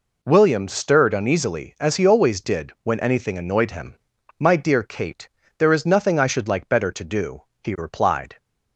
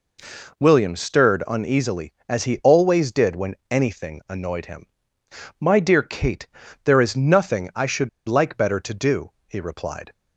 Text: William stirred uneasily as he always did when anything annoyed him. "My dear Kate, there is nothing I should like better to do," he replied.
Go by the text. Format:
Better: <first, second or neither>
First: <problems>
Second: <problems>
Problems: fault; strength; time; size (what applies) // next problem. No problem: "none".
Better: first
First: none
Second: pauses between "when" and "anything"; slight; at 3.5 s; 0.16 s long // pauses between "should" and "like"; slight; at 8.0 s; 0.19 s long